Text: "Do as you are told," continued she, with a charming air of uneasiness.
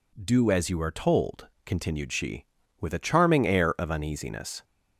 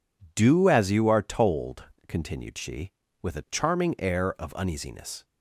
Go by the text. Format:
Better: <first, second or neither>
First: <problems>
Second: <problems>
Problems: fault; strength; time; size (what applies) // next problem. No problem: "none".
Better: neither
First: none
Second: none